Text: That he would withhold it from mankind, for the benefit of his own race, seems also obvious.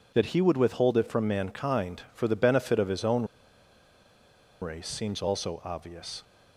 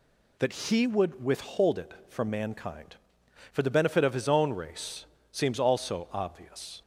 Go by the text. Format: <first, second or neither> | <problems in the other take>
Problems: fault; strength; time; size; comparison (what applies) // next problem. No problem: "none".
second | pauses between "own" and "race"; strong; at 3.2 s; 1.3 s long